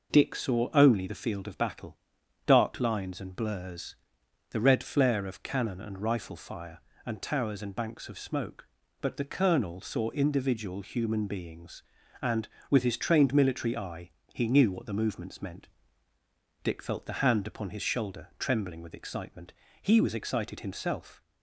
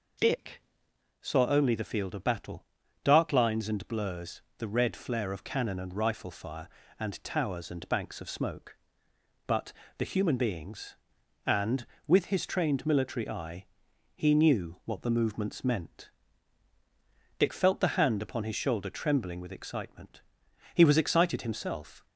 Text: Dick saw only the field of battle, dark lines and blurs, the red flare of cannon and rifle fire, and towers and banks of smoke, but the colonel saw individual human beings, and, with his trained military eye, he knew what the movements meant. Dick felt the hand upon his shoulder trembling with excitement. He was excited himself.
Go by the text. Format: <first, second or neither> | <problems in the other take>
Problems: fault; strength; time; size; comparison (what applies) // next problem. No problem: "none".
first | pauses between "Dick" and "saw"; noticeable; at 0.6 s; 0.60 s long // pauses between "but" and "the"; slight; at 9.7 s; 0.24 s long // skips "colonel saw individual"; at 10.0 s